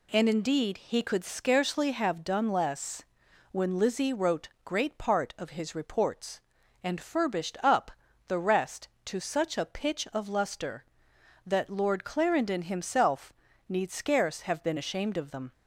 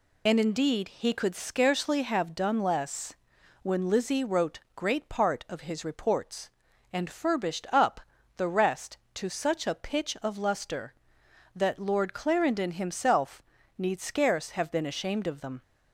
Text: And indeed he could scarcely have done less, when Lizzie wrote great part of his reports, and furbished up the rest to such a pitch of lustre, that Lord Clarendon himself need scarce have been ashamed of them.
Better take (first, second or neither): first